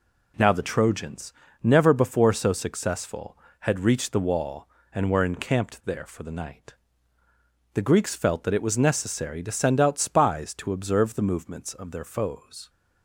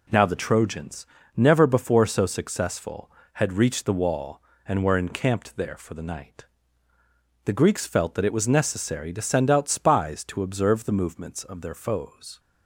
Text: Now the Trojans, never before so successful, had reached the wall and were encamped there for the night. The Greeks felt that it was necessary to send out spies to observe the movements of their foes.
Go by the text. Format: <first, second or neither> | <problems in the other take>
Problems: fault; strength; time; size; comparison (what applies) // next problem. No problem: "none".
neither | none